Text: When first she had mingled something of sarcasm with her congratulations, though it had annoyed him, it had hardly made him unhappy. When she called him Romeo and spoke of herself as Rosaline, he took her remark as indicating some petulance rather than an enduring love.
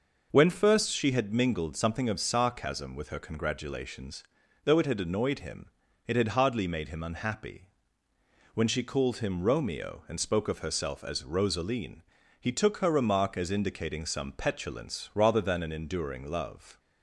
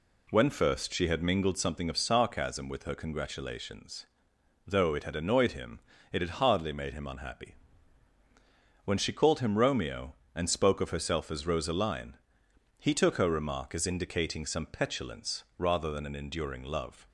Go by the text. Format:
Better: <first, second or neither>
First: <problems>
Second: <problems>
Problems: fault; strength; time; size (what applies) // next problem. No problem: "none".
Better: neither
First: none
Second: none